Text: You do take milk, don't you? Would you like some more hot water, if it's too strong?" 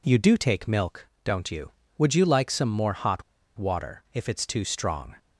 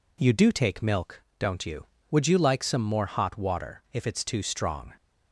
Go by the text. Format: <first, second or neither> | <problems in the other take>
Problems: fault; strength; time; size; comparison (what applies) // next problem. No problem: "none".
second | pauses between "hot" and "water"; slight; at 3.2 s; 0.35 s long